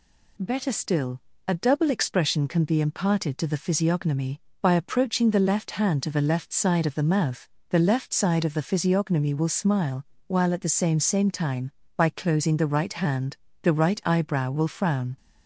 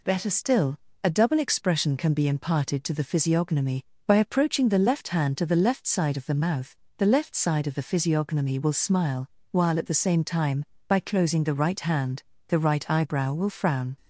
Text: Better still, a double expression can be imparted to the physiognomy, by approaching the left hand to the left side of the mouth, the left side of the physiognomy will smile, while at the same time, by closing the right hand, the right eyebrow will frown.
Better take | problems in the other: second | says "same" twice; at 11.0 s

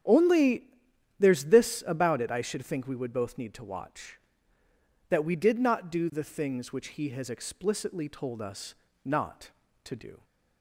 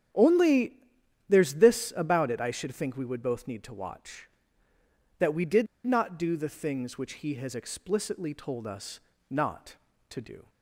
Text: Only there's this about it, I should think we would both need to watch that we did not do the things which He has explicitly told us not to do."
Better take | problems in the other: first | starts louder than the rest; strong; until 1.6 s; 9.5 dB; strong in the first // pauses between "Only" and "there's"; noticeable; at 0.7 s; 0.56 s long; noticeable in the first // pauses between "did" and "not"; slight; at 5.6 s; 0.18 s long // pauses between "us" and "not"; slight; at 8.9 s; 0.30 s long; slight in the first

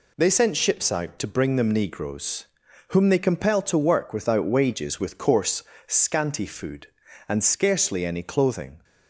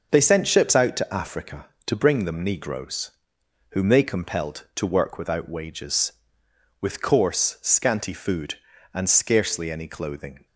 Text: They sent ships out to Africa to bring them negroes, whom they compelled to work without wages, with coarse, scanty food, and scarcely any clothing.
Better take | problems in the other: second | skips "Africa to"; at 1.2 s

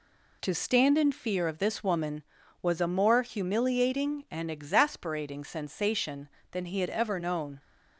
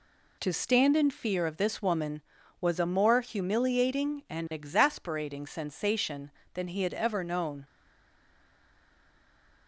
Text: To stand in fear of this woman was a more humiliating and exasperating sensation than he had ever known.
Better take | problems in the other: first | stays silent after the last word; noticeable; from 7.6 s on; 2.0 s long

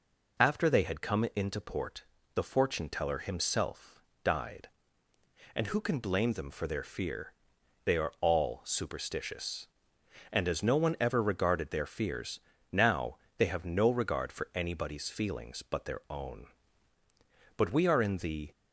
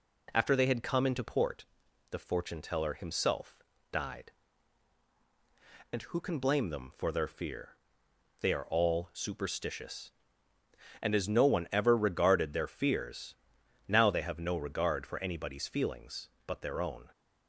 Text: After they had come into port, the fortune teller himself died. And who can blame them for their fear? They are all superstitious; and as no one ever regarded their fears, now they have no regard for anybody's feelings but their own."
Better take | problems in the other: second | pauses between "himself" and "died"; slight; at 4.0 s; 0.20 s long; slight in the second // pauses between "now" and "they"; slight; at 13.1 s; 0.22 s long // goes on to say "But we are in the"; noticeable; from 17.5 s on; 0.96 s long

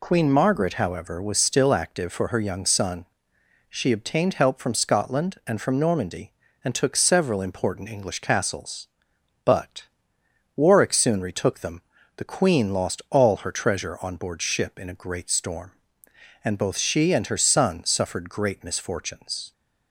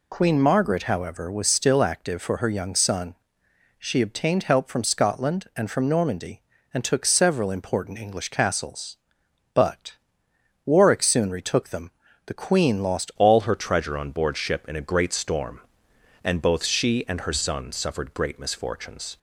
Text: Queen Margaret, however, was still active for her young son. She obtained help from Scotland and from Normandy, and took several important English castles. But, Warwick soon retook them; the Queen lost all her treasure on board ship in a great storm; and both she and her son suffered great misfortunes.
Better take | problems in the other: first | changes voice at "all"; from 13.1 s on; 6.0 s long

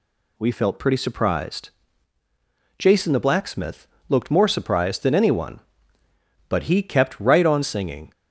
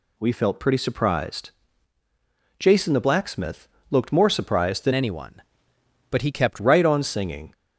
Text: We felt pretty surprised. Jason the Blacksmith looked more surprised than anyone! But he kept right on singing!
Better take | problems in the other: first | pauses between "Blacksmith" and "looked"; slight; at 3.6 s; 0.24 s long; slight in the first // changes voice from "anyone" to "kept"; from 4.9 to 6.5 s; 1.6 s long

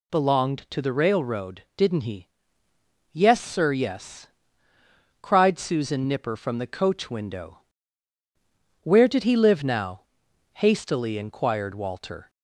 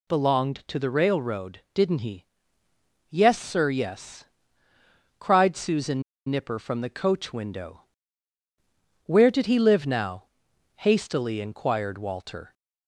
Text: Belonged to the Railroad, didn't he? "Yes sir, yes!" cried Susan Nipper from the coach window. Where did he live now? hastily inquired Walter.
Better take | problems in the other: first | pauses between "Susan" and "Nipper"; slight; at 6.0 s; 0.26 s long

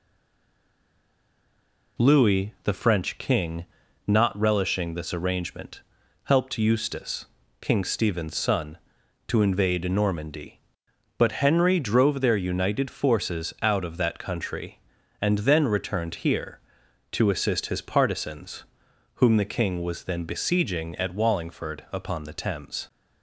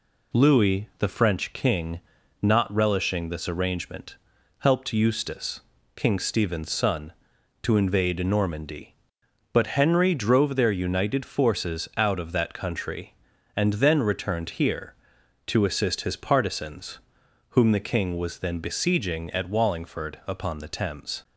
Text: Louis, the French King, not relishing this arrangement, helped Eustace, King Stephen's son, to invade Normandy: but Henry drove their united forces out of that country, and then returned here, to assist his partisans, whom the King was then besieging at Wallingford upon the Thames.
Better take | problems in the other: second | stays silent before the first word; noticeable; until 1.9 s; 1.9 s long

